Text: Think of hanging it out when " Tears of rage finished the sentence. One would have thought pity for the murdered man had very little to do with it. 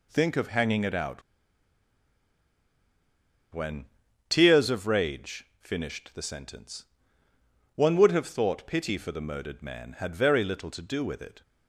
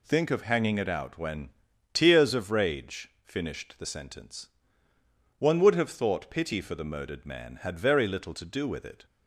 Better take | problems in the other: second | pauses between "out" and "when"; strong; at 1.2 s; 2.3 s long // pauses between "rage" and "finished"; slight; at 5.4 s; 0.16 s long; slight in the second

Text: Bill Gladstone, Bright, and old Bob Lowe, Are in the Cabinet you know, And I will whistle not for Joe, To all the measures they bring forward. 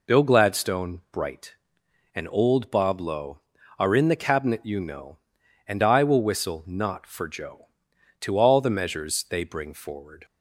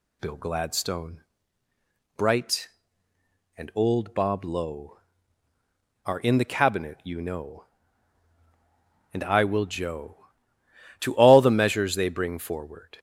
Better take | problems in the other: first | skips "whistle not for"; at 9.6 s

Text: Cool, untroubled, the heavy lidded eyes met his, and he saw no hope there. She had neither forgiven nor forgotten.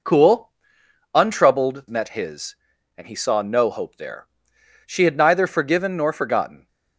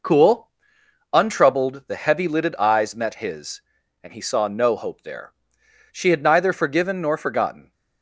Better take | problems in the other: second | skips "the heavy lidded eyes"; at 1.8 s

